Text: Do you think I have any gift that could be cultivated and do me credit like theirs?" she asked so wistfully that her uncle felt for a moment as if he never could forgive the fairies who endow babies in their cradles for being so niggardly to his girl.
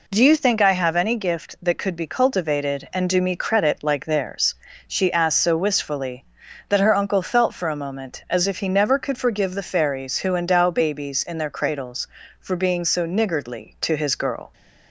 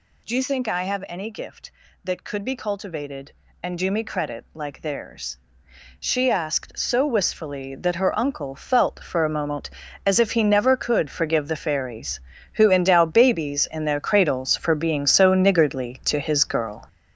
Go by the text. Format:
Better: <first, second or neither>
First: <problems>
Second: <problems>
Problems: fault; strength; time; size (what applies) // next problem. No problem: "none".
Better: first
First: none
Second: gets louder; strong; throughout; 8 dB